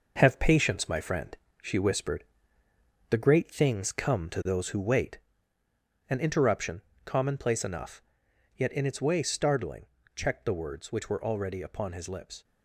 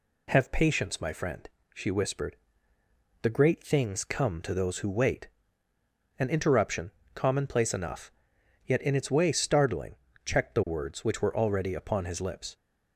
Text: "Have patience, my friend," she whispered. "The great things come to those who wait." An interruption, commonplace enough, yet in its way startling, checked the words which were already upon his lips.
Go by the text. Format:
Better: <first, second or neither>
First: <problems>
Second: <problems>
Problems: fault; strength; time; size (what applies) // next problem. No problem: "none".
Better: second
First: gets quieter; throughout; 6.5 dB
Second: none